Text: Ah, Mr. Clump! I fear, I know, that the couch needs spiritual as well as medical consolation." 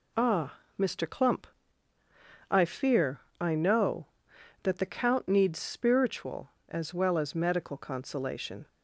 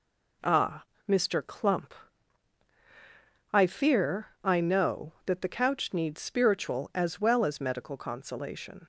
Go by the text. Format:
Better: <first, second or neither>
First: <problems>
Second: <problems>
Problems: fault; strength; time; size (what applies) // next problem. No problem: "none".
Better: second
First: says "count" for "couch"; at 4.8 s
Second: none